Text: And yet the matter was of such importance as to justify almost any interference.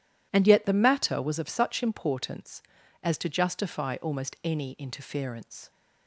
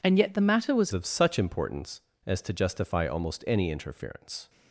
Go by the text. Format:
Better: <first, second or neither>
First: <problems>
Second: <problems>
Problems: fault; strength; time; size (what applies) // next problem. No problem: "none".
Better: first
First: none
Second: changes voice at "of"; from 0.9 s on; 3.5 s long